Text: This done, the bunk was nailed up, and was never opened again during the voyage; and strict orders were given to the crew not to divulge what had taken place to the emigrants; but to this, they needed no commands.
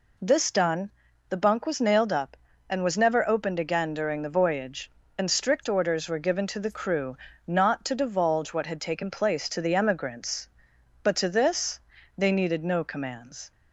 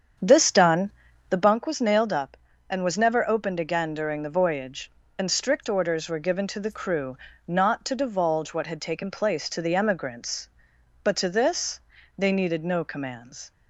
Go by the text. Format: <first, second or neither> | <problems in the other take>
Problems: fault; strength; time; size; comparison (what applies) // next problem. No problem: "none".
first | starts louder than the rest; strong; until 1.6 s; 8 dB // pauses between "crew" and "not"; slight; at 7.1 s; 0.30 s long; slight in the first